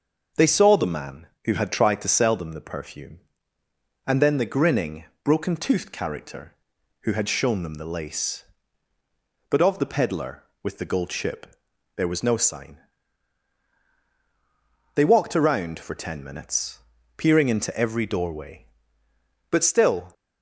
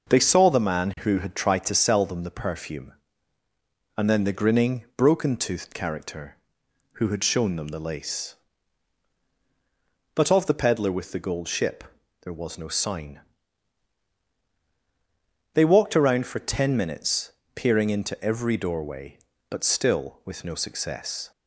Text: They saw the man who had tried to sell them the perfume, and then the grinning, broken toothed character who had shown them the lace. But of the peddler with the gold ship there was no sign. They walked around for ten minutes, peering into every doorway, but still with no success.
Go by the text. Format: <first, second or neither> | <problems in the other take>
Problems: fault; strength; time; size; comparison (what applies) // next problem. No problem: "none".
second | starts louder than the rest; noticeable; until 1.5 s; 6 dB // pauses between "ship" and "there"; noticeable; at 11.4 s; 0.50 s long; also in the second // stops before "with no success"; at 20.1 s